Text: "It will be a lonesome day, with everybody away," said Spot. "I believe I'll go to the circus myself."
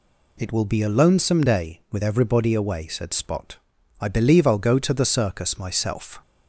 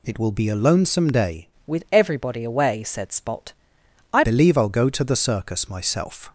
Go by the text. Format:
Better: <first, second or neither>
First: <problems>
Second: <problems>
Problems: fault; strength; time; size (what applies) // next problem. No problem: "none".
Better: first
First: none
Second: changes voice from "with" to "I"; from 1.6 to 4.2 s; 2.6 s long